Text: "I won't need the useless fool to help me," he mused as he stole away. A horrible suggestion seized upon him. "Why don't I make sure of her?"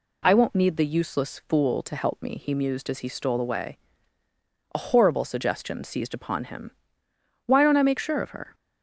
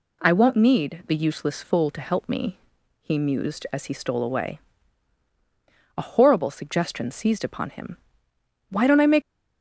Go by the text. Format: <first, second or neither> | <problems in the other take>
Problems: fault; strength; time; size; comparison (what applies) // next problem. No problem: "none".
first | stops before "sure of her"; at 9.2 s